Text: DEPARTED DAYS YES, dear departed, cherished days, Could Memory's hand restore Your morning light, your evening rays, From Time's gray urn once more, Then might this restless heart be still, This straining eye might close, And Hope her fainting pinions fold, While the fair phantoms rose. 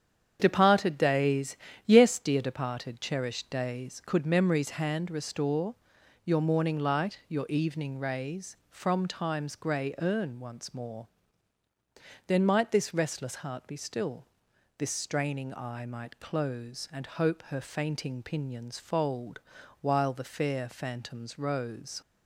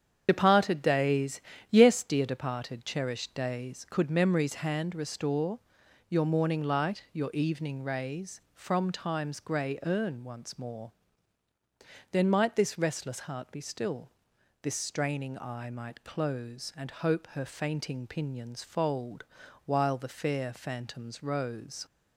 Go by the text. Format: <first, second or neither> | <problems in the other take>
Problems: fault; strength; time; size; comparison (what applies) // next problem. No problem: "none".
first | loses the start of "DEPARTED"; at 0.2 s; 45 ms // starts louder than the rest; strong; until 1.2 s; 8 dB; strong in the first // pauses between "DAYS" and "YES"; slight; at 1.3 s; 0.30 s long; slight in the first // pauses between "restore" and "Your"; noticeable; at 5.5 s; 0.50 s long; noticeable in the first